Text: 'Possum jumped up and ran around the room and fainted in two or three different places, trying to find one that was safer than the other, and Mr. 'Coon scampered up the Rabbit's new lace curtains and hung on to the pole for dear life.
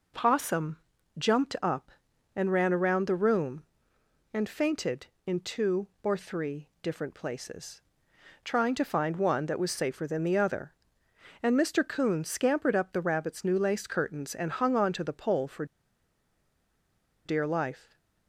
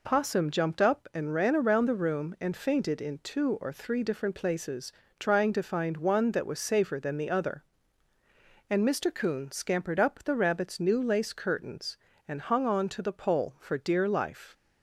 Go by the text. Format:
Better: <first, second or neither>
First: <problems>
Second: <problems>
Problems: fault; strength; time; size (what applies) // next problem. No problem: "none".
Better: second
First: pauses between "Possum" and "jumped"; at 0.7 s; 0.42 s long // pauses between "for" and "dear"; strong; at 15.6 s; 1.6 s long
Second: none